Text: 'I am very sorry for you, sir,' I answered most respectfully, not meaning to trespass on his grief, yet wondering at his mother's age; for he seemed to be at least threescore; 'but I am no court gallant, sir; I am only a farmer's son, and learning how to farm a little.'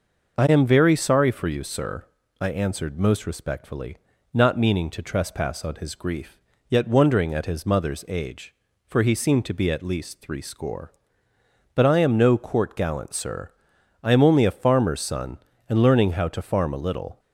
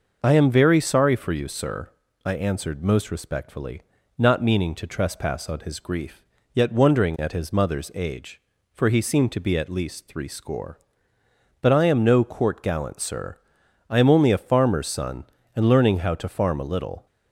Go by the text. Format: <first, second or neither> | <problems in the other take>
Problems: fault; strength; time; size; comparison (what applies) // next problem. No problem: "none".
neither | none